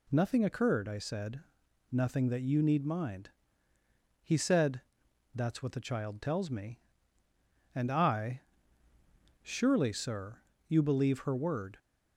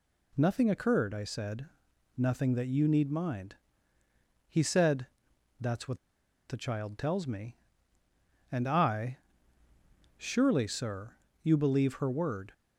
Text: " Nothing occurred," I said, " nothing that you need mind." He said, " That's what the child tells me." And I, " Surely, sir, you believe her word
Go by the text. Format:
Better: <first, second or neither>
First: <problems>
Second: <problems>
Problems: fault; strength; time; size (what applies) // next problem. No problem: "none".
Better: first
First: none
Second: pauses between "what" and "the"; noticeable; at 5.9 s; 0.51 s long